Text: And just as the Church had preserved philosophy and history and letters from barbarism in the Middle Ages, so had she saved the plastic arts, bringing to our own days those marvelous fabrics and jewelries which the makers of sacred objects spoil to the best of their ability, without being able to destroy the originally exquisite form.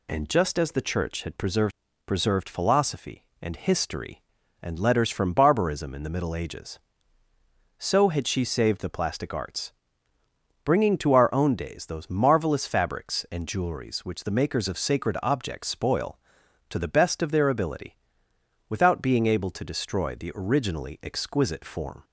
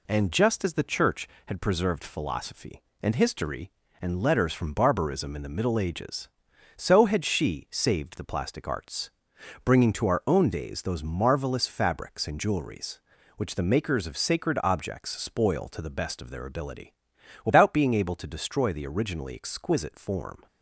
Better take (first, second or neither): second